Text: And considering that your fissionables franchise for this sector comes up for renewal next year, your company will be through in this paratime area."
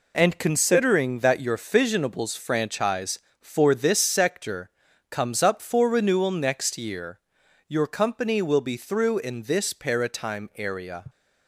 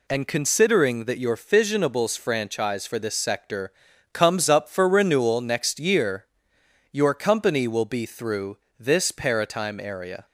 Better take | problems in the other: first | pauses between "sector" and "comes"; at 3.7 s; 0.42 s long; also in the first // skips "in"; at 8.6 s

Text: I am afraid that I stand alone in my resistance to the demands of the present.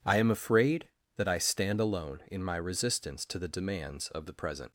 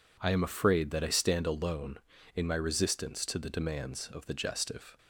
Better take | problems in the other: first | says "gestive" for "present"; at 4.3 s

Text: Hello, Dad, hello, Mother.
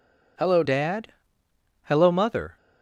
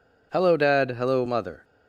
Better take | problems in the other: second | changes voice at "Dad"; from 0.6 s on; 1.9 s long

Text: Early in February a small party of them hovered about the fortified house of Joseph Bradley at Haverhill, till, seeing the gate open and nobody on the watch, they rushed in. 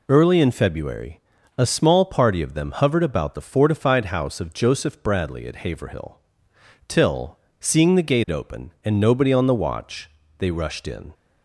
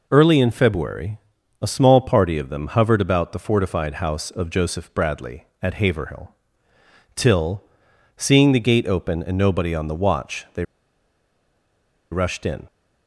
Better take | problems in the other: first | pauses between "February" and "a"; at 1.1 s; 0.42 s long; slight in the first // pauses between "they" and "rushed"; strong; at 10.6 s; 1.4 s long

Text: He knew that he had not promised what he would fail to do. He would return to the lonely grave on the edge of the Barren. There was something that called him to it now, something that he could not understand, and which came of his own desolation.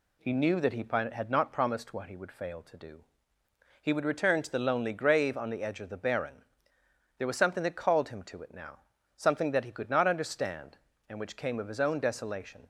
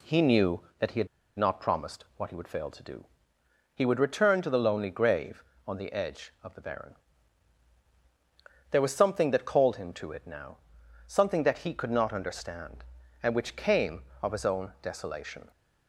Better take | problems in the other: first | pauses between "had" and "not"; slight; at 1.0 s; 0.31 s long

